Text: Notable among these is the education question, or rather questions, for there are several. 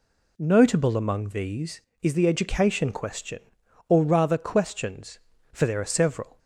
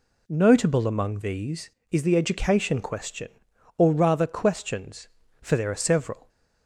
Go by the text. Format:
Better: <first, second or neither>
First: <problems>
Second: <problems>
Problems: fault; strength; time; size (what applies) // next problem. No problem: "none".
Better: neither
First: none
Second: none